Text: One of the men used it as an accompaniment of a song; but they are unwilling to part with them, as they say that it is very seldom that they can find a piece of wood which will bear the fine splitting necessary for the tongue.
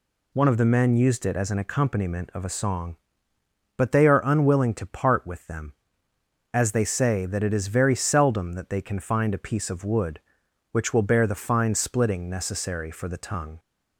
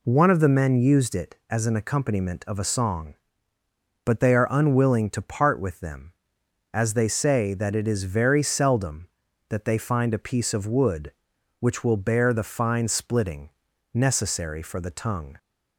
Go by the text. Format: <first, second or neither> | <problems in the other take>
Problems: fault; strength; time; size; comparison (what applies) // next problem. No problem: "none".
first | skips "can"; at 9.7 s // pauses between "splitting" and "necessary"; at 13.4 s; 0.44 s long